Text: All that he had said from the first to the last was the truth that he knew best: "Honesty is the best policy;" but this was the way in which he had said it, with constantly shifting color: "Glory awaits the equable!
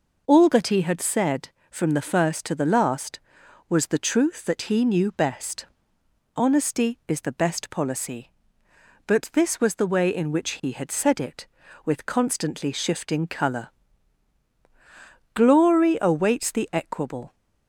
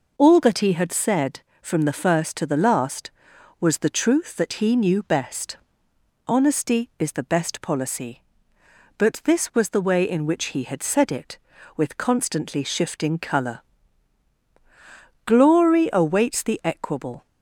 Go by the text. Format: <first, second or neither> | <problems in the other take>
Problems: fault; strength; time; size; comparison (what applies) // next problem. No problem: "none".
neither | none